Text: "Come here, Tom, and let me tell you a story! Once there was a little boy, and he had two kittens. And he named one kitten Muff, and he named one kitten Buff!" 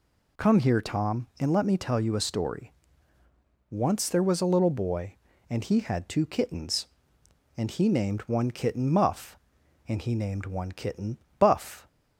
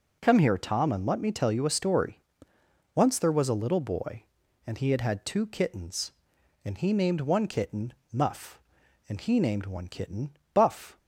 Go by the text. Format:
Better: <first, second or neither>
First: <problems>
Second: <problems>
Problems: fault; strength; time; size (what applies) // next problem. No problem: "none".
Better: first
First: pauses between "kitten" and "Buff"; slight; at 11.1 s; 0.22 s long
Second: says "had" twice; at 5.0 s // pauses between "kitten" and "Muff"; slight; at 7.9 s; 0.20 s long // pauses between "kitten" and "Buff"; slight; at 10.3 s; 0.24 s long